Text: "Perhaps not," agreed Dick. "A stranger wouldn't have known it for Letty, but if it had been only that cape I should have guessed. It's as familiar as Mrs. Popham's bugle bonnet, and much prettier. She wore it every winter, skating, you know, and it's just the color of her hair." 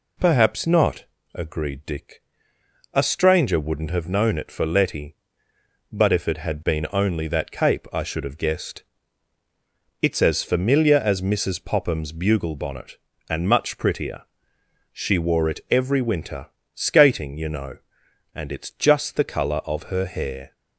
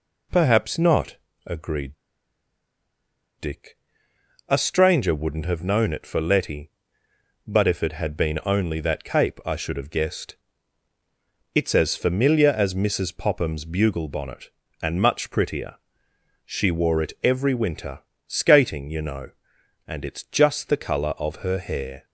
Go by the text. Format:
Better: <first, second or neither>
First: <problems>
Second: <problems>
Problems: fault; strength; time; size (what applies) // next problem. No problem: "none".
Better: first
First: none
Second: pauses between "agreed" and "Dick"; strong; at 1.9 s; 1.4 s long